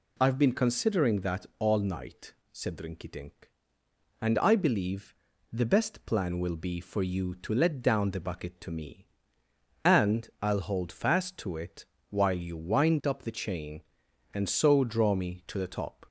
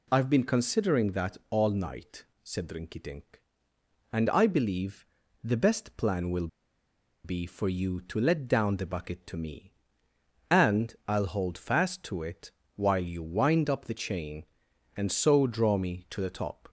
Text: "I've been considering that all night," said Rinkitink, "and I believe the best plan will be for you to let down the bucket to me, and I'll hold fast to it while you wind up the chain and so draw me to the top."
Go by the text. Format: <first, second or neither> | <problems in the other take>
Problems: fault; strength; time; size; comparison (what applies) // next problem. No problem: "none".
first | pauses between "believe" and "the"; at 5.0 s; 0.38 s long; also in the first // pauses between "will" and "be"; noticeable; at 6.4 s; 0.77 s long // pauses between "it" and "while"; slight; at 12.5 s; 0.24 s long; slight in the first